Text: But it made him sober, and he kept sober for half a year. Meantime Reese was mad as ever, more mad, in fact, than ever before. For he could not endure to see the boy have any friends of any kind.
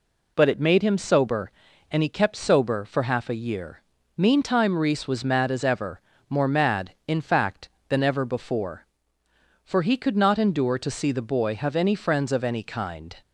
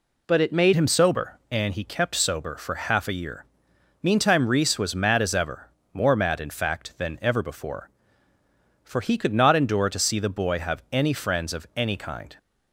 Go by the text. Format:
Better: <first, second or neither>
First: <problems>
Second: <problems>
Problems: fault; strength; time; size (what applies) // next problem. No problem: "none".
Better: first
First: none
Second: changes voice at "him"; from 0.7 s on; 11.6 s long